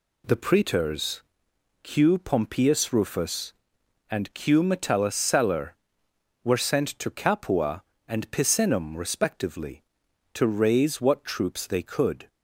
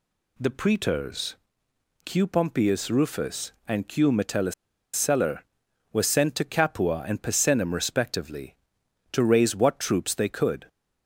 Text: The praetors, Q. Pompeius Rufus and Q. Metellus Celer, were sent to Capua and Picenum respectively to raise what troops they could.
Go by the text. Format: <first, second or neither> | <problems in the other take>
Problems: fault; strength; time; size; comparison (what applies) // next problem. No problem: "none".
first | pauses between "Metellus" and "Celer"; at 4.5 s; 0.41 s long